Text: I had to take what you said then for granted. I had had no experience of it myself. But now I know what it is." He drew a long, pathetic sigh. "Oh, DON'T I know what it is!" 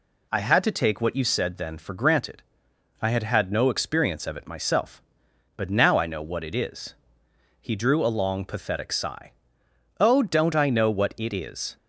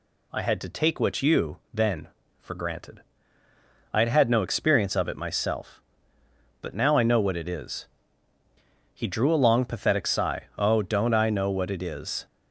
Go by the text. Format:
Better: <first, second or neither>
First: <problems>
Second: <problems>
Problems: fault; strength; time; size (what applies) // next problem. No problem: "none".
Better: first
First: none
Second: skips "said"; at 1.6 s